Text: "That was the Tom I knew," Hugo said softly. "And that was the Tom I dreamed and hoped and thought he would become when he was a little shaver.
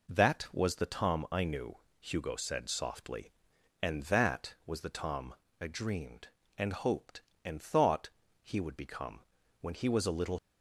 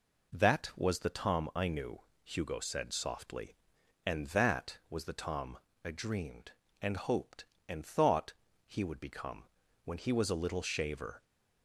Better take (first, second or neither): second